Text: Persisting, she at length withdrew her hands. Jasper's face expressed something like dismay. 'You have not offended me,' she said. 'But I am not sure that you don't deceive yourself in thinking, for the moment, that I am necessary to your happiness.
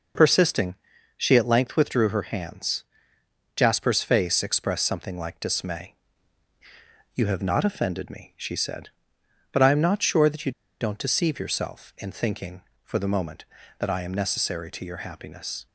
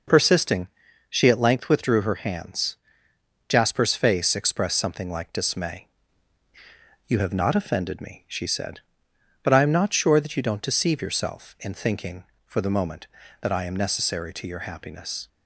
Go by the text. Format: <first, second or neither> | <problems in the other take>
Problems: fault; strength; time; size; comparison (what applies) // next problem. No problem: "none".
second | pauses between "you" and "don't"; slight; at 10.5 s; 0.28 s long